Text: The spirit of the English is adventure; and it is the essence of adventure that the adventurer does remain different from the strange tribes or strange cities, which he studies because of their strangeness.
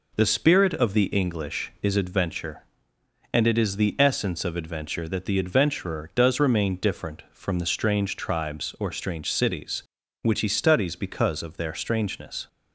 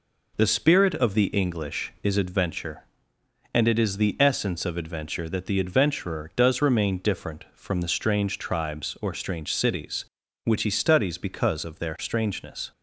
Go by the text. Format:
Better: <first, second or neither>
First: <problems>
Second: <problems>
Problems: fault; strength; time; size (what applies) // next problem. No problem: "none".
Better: neither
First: none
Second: none